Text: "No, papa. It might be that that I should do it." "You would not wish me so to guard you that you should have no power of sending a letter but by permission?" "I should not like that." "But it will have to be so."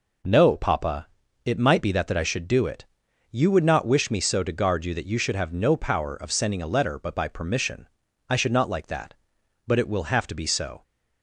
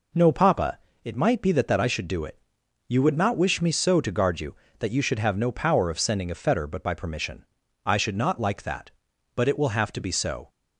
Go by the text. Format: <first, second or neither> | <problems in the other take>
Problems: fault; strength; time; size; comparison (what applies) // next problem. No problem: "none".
first | says "fetter" for "letter"; at 6.3 s